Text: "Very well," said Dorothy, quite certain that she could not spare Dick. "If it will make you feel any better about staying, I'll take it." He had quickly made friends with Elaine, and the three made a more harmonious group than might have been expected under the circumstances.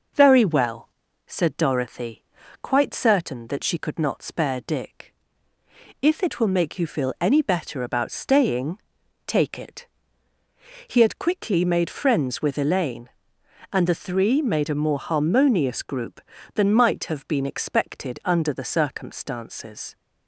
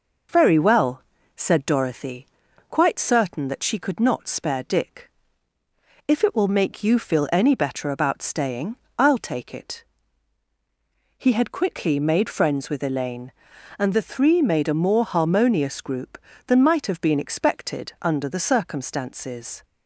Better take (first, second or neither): second